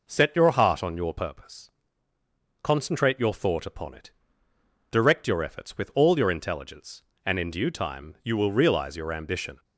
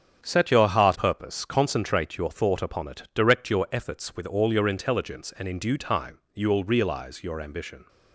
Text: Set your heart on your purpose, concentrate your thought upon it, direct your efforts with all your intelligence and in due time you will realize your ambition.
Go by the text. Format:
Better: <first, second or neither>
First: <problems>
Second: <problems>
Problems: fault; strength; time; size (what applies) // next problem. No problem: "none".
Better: first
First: none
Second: starts louder than the rest; strong; until 1.2 s; 8.5 dB // skips "on your"; at 0.9 s // pauses between "time" and "you"; slight; at 6.1 s; 0.16 s long